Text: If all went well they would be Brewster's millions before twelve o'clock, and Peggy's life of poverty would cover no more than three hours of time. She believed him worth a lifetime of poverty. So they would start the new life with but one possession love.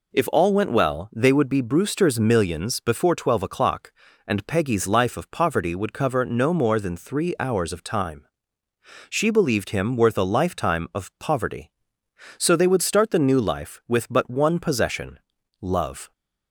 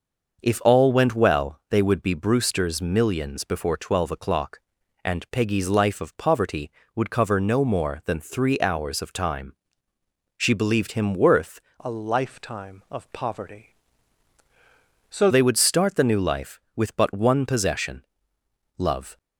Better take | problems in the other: first | starts louder than the rest; until 1.4 s; 6 dB // changes voice from "a" to "So"; from 11.8 to 15.2 s; 3.4 s long // pauses between "possession" and "love"; noticeable; at 18.0 s; 0.74 s long; also in the first

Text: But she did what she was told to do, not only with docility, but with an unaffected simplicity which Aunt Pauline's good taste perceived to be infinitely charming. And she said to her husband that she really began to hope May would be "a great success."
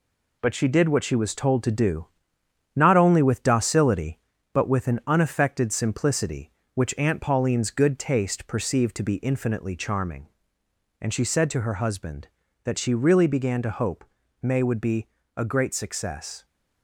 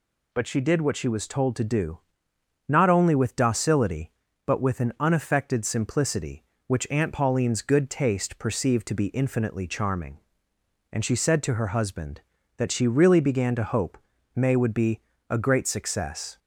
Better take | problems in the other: second | gets quieter; noticeable; throughout; 5.5 dB // pauses between "hope" and "May"; at 14.0 s; 0.38 s long; also in the second // pauses between "be" and "a"; slight; at 15.0 s; 0.28 s long; slight in the second

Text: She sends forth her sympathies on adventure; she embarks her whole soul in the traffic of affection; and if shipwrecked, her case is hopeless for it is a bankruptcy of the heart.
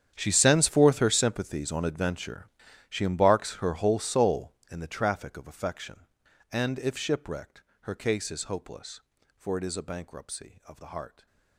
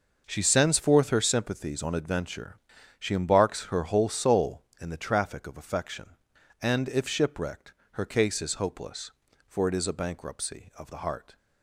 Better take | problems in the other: second | gets quieter; strong; throughout; 18.5 dB

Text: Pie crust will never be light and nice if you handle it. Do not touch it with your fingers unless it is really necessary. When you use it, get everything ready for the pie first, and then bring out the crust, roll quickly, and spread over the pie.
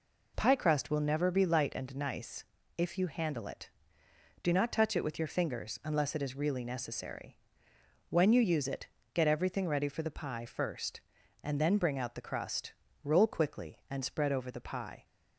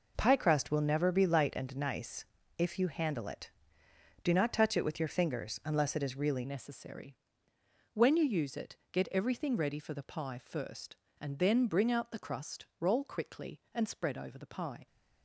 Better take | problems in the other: first | pauses between "nice" and "if"; slight; at 2.2 s; 0.34 s long; slight in the first // changes voice at "necessary"; from 6.4 s on; 8.4 s long

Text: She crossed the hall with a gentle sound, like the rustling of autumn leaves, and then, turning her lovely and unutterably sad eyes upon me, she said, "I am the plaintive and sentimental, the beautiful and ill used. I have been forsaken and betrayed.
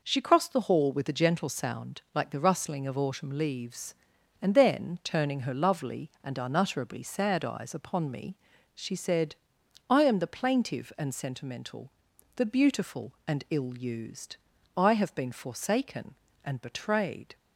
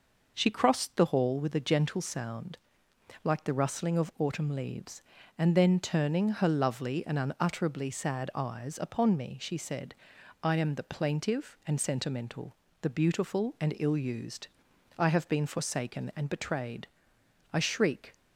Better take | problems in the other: first | goes on to say "I shriek"; from 17.5 s on; 0.60 s long

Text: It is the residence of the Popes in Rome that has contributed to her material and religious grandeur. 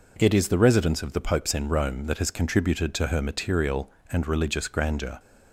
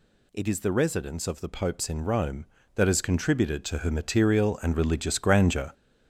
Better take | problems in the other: first | gets louder; throughout; 7 dB

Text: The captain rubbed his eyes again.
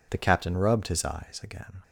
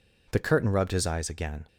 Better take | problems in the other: first | says "curtain" for "captain"; at 0.3 s

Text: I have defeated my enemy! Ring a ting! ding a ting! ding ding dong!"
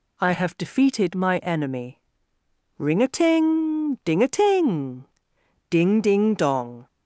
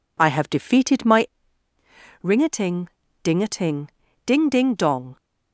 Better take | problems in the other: first | skips "enemy"; at 1.7 s

